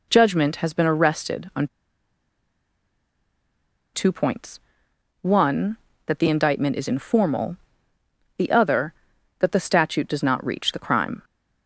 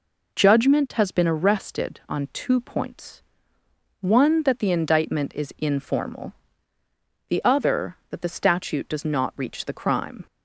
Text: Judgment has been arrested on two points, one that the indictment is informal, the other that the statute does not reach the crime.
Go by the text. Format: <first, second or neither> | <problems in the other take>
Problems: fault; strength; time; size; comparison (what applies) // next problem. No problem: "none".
second | pauses between "on" and "two"; strong; at 1.6 s; 2.2 s long